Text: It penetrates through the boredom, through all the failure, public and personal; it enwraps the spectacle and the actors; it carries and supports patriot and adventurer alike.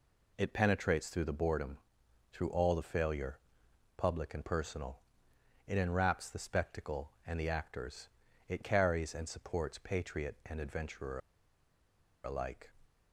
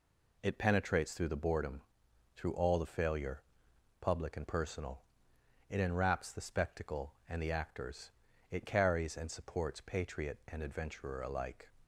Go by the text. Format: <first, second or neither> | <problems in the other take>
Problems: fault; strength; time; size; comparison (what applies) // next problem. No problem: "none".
second | pauses between "adventurer" and "alike"; at 11.1 s; 1.0 s long